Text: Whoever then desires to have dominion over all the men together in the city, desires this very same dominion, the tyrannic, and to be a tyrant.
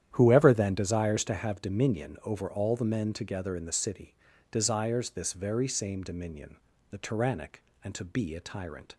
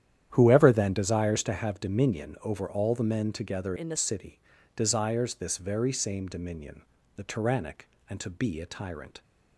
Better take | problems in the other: first | starts louder than the rest; strong; until 1.3 s; 10.5 dB; strong in the first // changes voice from "in" to "the"; from 3.7 to 3.9 s; 0.2 s long

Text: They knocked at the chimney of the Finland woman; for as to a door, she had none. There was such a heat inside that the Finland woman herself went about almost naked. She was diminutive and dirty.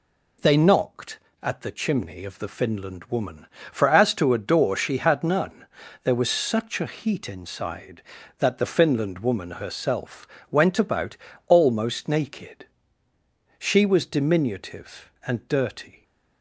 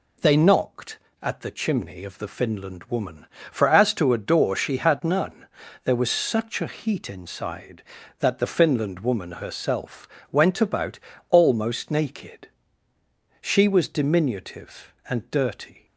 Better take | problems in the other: neither | pauses between "herself" and "went"; slight; the same in both // pauses between "about" and "almost"; slight; the same in both

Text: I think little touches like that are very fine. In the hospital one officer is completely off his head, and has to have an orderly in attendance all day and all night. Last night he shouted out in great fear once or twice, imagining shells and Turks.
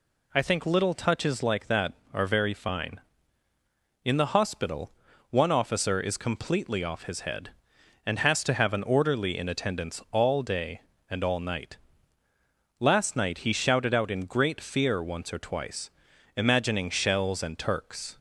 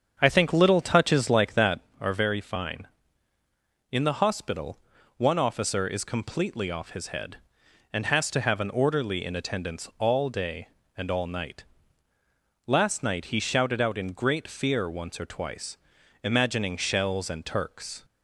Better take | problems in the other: first | starts louder than the rest; strong; until 1.8 s; 7.5 dB // pauses between "hospital" and "one"; at 4.7 s; 0.38 s long; also in the first

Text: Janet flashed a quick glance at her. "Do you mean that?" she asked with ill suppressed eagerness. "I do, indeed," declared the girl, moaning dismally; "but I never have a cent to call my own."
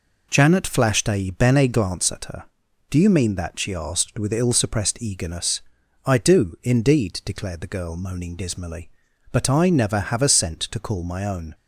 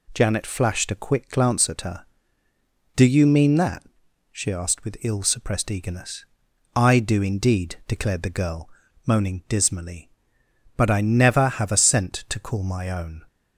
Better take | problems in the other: second | says "bene" for "quick"; at 1.3 s

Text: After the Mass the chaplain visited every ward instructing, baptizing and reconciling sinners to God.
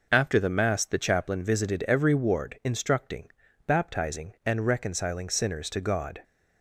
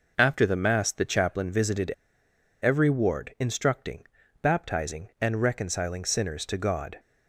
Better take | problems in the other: first | pauses between "visited" and "every"; noticeable; at 1.9 s; 0.71 s long

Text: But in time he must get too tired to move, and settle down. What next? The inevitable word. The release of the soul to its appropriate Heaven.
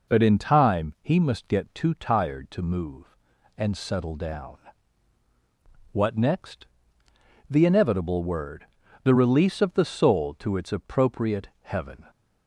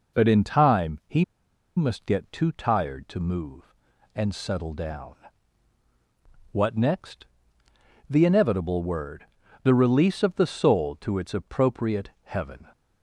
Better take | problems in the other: first | pauses between "he" and "must"; noticeable; at 1.2 s; 0.52 s long

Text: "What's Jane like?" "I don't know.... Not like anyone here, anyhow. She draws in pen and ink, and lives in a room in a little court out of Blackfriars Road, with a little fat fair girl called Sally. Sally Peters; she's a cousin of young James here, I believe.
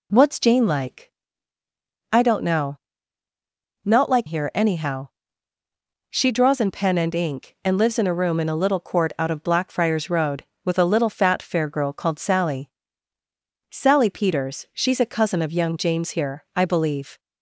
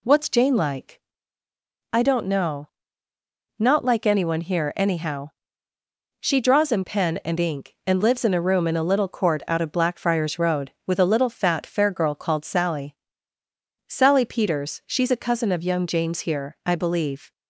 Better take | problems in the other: second | skips "anyone"; at 4.2 s

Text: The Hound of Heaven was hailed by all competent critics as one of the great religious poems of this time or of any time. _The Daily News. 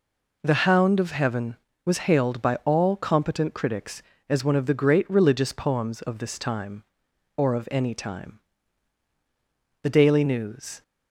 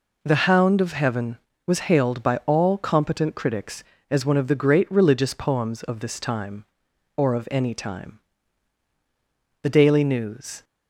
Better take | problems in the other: neither | none

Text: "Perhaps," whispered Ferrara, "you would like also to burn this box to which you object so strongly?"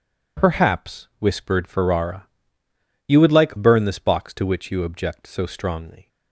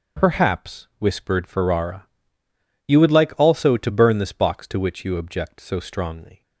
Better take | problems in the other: second | skips "also to"; at 3.5 s

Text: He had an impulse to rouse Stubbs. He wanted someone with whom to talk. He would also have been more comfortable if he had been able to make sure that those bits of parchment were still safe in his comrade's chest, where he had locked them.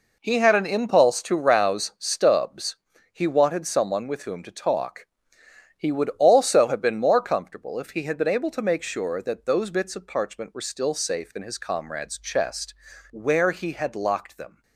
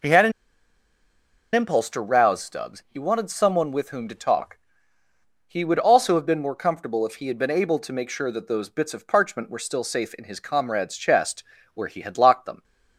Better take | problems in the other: first | pauses between "an" and "impulse"; at 0.3 s; 1.2 s long

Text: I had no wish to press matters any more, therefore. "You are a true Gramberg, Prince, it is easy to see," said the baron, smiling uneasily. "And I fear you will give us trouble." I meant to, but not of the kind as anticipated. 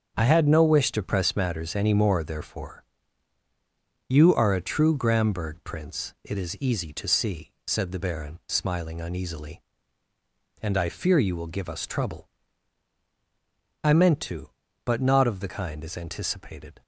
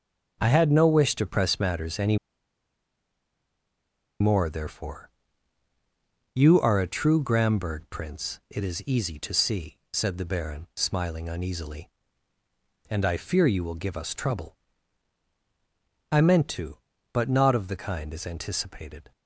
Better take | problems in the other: first | starts louder than the rest; until 1.4 s; 6.5 dB; also in the first // pauses between "any" and "more"; strong; at 2.1 s; 2.0 s long

